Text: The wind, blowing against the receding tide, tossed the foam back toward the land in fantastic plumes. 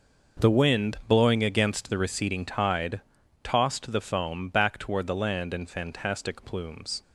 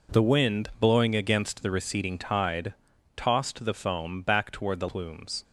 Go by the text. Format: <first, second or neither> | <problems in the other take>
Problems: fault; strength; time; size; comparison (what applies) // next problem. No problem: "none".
first | skips "land in fantastic"; at 4.8 s